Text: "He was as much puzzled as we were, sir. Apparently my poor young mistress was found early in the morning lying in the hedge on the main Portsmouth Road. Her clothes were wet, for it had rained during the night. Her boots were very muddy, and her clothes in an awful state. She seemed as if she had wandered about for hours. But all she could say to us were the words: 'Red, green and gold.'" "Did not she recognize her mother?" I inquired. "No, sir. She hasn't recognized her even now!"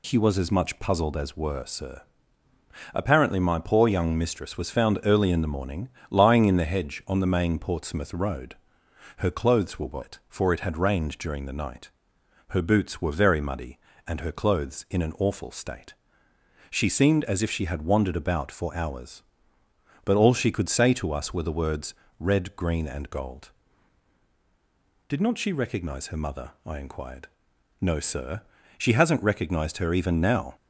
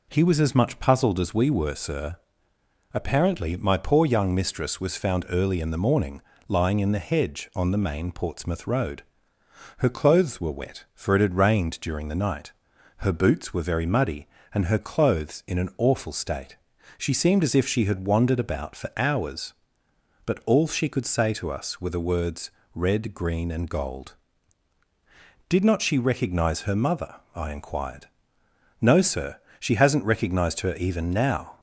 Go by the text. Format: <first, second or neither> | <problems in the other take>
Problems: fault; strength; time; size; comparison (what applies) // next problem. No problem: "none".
second | skips "we"; at 1.3 s // pauses between "morning" and "lying"; slight; at 5.8 s; 0.22 s long; slight in the second